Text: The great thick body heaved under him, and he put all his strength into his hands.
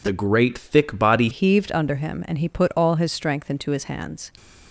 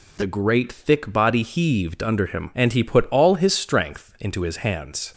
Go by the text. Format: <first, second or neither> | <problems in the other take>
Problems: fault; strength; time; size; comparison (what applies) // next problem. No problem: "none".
second | changes voice at "heaved"; from 1.3 s on; 3.0 s long